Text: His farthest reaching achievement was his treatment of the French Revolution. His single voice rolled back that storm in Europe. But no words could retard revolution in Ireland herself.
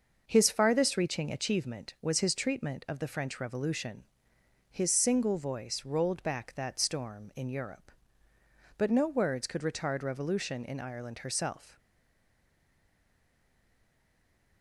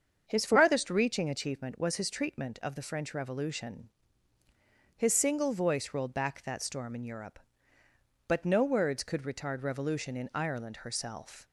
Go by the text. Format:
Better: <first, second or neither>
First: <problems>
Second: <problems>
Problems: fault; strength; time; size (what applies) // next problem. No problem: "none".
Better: second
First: starts louder than the rest; noticeable; until 1.2 s; 6 dB // stays silent after the last word; strong; from 11.7 s on; 2.9 s long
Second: starts louder than the rest; strong; until 1.2 s; 7 dB